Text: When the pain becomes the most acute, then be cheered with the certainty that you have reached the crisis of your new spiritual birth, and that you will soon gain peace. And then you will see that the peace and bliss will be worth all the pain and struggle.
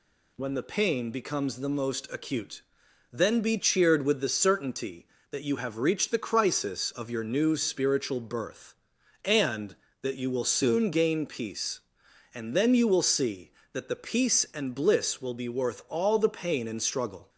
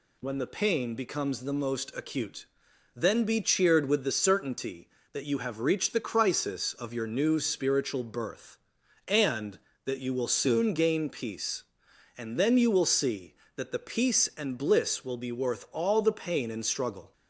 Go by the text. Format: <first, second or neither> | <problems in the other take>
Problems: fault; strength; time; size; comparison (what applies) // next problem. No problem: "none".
neither | none